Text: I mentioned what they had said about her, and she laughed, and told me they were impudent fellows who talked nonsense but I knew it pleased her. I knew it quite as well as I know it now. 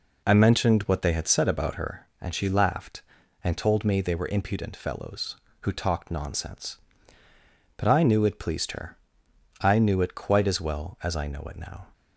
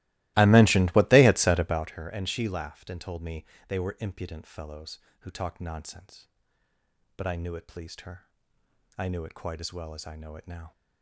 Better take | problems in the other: first | starts louder than the rest; strong; until 1.9 s; 18.5 dB // pauses between "me" and "they"; slight; at 3.4 s; 0.22 s long

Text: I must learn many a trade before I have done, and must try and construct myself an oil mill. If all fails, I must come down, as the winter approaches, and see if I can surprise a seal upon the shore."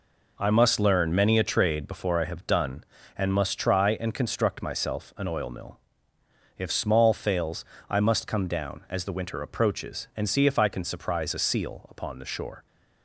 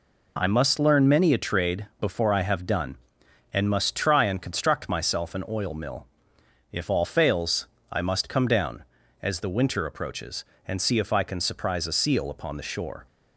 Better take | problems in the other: second | says "small" for "all"; at 6.7 s

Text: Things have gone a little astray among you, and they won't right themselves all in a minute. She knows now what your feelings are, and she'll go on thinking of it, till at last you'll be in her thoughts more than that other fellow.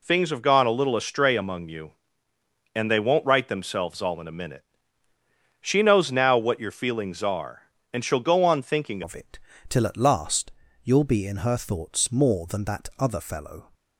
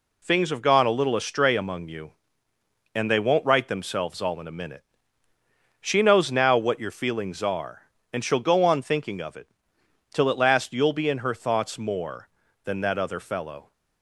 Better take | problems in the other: second | changes voice at "of"; from 9.0 s on; 4.7 s long // pauses between "last" and "you'll"; slight; at 10.5 s; 0.32 s long

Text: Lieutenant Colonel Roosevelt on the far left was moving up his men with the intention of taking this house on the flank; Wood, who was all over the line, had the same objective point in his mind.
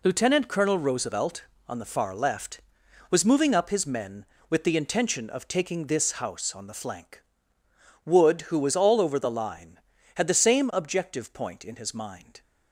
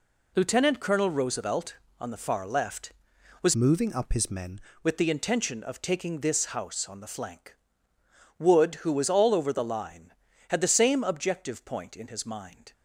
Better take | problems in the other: first | changes voice from "moving" to "men"; from 3.5 to 4.5 s; 1.0 s long

